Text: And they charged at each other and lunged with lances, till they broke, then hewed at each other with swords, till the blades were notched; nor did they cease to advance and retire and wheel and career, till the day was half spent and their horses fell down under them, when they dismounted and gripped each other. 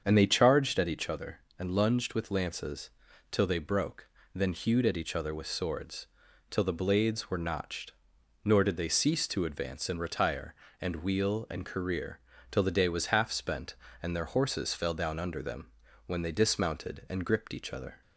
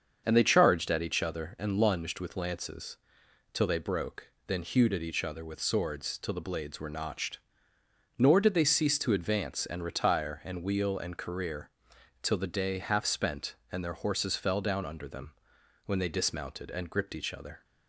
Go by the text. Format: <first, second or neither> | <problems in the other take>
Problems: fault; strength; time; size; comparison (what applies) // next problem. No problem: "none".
first | starts louder than the rest; until 1.2 s; 7 dB; strong in the first // skips "was"; at 12.7 s